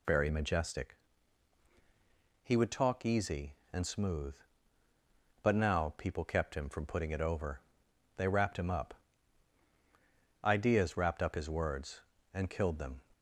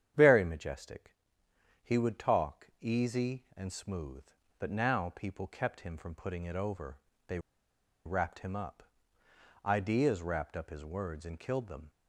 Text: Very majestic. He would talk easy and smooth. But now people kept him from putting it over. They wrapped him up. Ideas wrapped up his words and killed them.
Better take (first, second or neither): first